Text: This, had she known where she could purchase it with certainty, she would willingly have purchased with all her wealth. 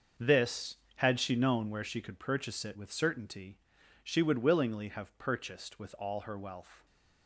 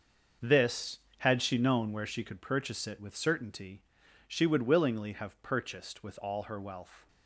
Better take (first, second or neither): neither